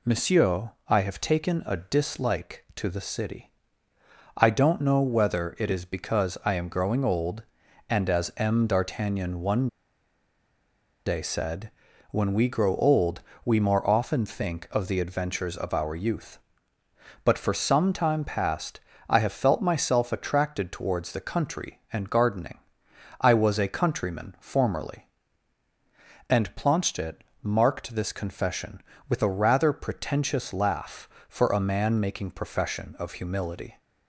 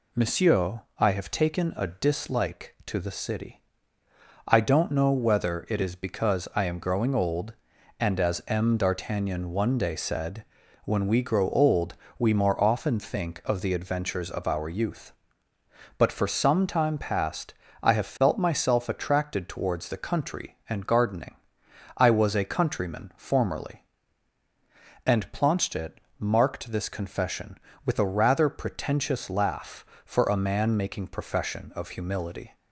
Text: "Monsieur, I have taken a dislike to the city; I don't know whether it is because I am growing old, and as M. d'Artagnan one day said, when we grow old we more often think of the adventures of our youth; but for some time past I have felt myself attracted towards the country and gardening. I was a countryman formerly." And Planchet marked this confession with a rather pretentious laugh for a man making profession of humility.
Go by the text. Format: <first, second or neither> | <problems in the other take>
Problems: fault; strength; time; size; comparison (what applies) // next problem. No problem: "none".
second | pauses between "one" and "day"; strong; at 9.6 s; 1.3 s long // pauses between "old" and "we"; slight; at 13.1 s; 0.24 s long; slight in the second // pauses between "past" and "I"; slight; at 18.7 s; 0.28 s long; slight in the second // pauses between "Planchet" and "marked"; slight; at 27.2 s; 0.22 s long; slight in the second